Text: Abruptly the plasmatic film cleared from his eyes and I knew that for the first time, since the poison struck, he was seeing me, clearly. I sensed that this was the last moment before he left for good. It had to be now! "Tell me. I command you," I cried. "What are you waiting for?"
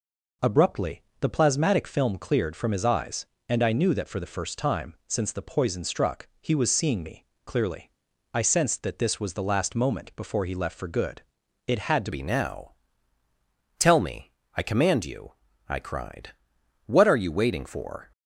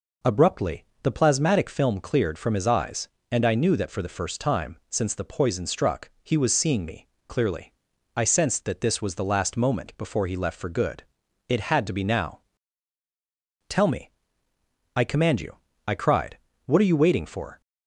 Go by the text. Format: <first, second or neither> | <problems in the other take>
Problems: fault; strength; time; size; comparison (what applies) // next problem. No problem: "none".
second | pauses between "Abruptly" and "the"; slight; at 1.0 s; 0.18 s long; slight in the second // changes voice at "be"; from 12.1 s on; 6.0 s long